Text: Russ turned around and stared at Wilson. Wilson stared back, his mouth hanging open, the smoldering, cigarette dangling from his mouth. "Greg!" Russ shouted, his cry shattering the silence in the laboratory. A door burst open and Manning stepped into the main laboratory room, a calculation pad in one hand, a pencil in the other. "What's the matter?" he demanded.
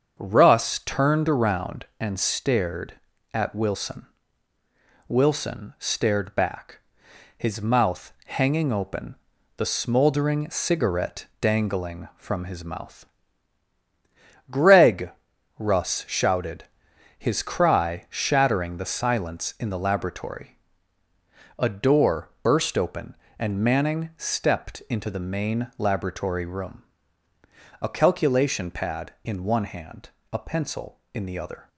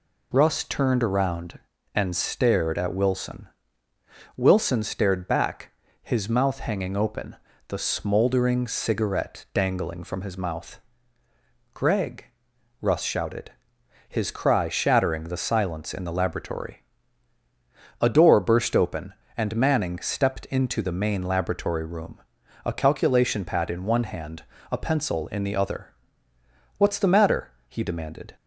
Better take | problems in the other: second | starts louder than the rest; until 1.1 s; 7 dB // stops before "What's the matter he demanded"; at 31.6 s

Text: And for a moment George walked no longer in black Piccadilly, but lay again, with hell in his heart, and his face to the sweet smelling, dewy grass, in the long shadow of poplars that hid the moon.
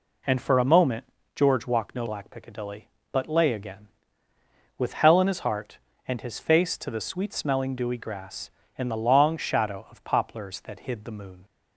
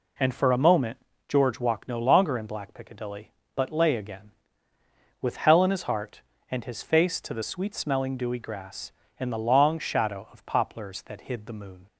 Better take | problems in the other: second | pauses between "moment" and "George"; slight; at 1.0 s; 0.30 s long; slight in the second // skips "longer in"; at 2.0 s

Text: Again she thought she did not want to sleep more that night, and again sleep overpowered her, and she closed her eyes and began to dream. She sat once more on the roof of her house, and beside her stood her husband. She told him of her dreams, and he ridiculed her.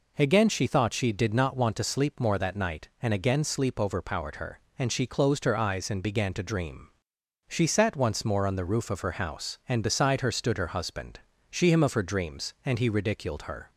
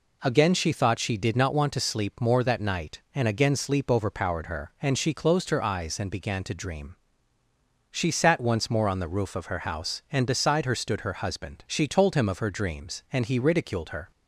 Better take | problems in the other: second | skips "told"; at 11.7 s

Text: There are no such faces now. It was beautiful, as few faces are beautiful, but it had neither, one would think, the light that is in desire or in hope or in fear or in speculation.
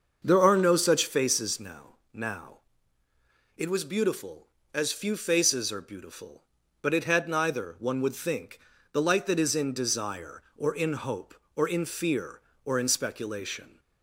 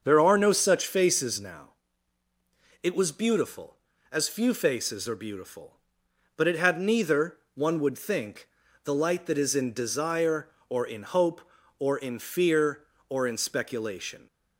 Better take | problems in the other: second | starts louder than the rest; until 1.2 s; 6.5 dB; also in the second // says "now" twice; at 2.1 s

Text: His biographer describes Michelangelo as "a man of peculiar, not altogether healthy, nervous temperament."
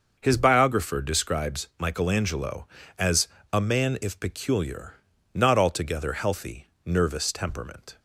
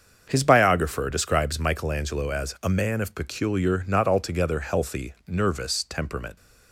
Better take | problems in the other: second | starts louder than the rest; until 1.2 s; 6.5 dB; also in the second // pauses between "as" and "a"; slight; at 3.2 s; 0.25 s long // says "if" for "of"; at 4.0 s

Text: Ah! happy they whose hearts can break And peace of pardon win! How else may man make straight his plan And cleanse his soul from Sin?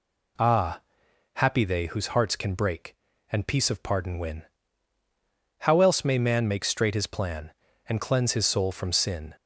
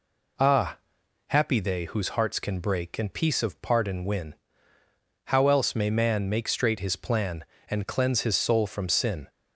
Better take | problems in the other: neither | none

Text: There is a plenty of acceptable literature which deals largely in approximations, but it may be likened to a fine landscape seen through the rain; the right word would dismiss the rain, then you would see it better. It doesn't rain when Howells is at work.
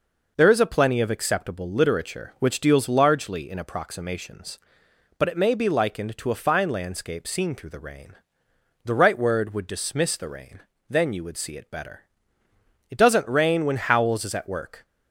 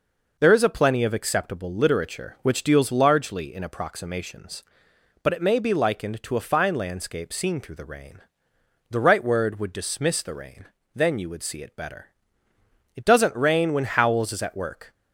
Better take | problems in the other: neither | none

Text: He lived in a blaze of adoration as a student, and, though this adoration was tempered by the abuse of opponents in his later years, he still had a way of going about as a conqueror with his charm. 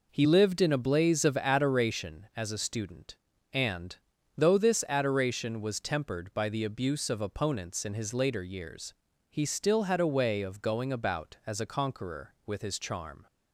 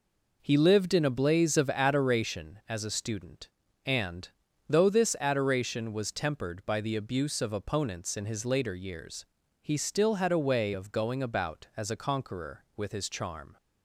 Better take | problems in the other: neither | none

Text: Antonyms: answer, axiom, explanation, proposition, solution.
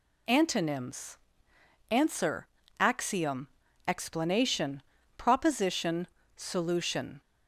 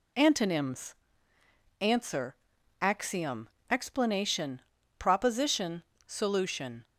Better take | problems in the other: neither | none

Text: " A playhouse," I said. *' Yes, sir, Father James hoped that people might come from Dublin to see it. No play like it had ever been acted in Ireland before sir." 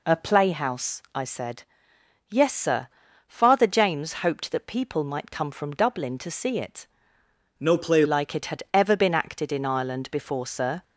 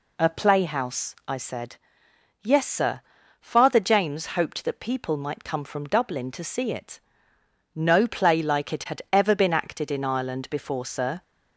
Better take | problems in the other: second | changes voice from "No" to "play"; from 7.5 to 8.0 s; 0.5 s long

